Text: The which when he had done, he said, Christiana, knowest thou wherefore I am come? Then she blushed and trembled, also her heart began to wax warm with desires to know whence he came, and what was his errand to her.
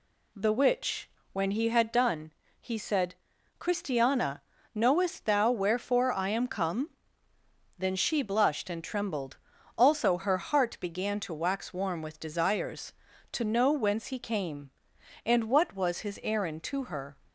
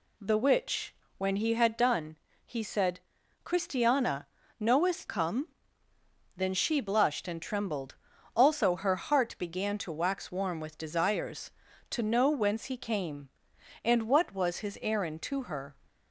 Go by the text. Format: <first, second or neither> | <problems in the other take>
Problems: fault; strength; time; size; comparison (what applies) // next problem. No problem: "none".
first | pauses between "which" and "when"; slight; at 0.9 s; 0.22 s long; slight in the first // skips "thou wherefore I am"; at 5.0 s